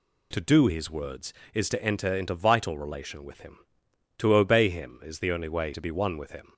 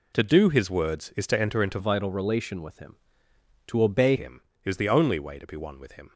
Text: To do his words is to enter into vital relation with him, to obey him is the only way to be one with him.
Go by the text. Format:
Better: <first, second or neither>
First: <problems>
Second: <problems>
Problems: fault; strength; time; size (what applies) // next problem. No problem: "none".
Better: first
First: none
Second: changes voice from "vital" to "obey"; from 1.7 to 4.1 s; 2.4 s long